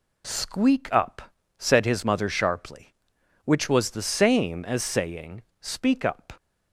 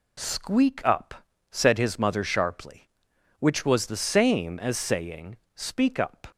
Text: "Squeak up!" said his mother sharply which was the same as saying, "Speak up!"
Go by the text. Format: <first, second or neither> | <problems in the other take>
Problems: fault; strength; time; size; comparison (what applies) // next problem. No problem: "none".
neither | none